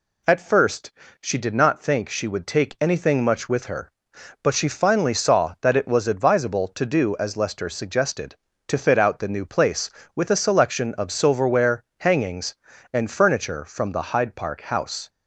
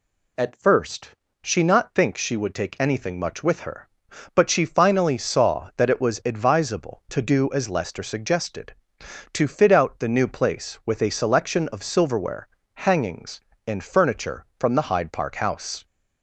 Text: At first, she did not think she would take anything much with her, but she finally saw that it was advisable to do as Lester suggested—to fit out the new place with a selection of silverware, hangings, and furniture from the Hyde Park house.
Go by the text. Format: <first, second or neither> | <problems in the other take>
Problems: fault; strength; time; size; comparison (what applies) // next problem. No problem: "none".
first | skips "did"; at 1.6 s